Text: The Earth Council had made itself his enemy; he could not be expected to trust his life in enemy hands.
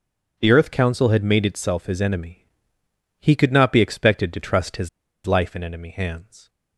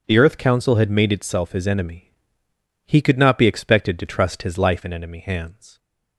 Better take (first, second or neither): second